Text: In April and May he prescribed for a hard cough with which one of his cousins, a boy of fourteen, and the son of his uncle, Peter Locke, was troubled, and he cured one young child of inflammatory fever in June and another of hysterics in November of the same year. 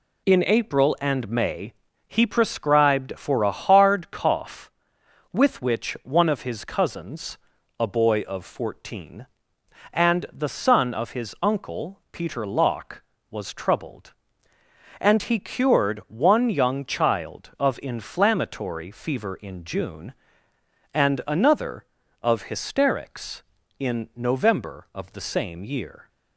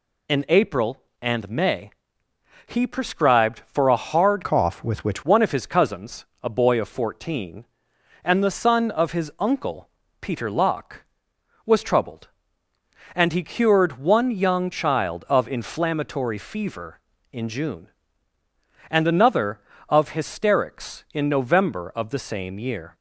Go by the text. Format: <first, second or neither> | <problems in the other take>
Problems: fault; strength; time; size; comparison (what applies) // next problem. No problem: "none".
first | pauses between "May" and "he"; noticeable; at 1.8 s; 0.76 s long; slight in the first // changes voice from "cough" to "which"; from 4.4 to 5.2 s; 0.8 s long